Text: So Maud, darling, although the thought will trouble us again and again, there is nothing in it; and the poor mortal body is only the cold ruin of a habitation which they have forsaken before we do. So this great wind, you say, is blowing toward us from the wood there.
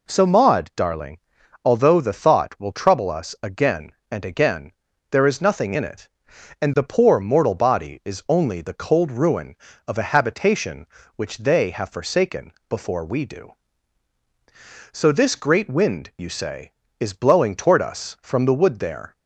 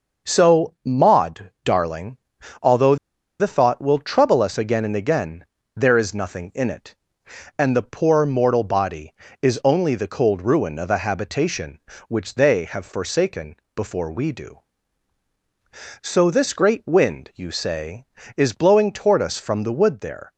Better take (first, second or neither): first